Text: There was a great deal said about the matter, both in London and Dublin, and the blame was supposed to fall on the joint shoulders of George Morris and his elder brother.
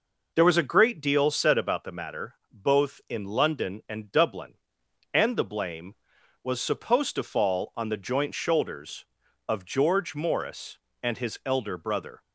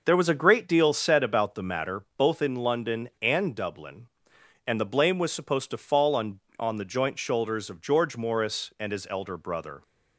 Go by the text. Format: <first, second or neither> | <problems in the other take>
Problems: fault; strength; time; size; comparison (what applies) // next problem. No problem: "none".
first | says "on" twice; at 6.6 s